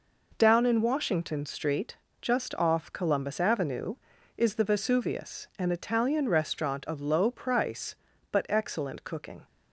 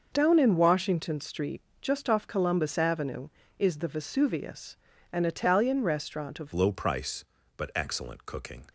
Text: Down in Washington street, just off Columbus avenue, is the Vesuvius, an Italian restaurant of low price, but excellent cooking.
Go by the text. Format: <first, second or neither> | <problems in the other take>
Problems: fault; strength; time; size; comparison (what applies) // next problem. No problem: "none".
first | changes voice at "low"; from 6.5 s on; 2.1 s long